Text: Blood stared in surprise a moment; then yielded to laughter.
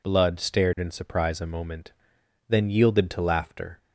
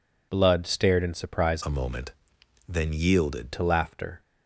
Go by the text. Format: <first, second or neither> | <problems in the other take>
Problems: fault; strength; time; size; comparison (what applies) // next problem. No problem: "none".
first | changes voice from "a" to "yielded"; from 1.6 to 3.5 s; 1.9 s long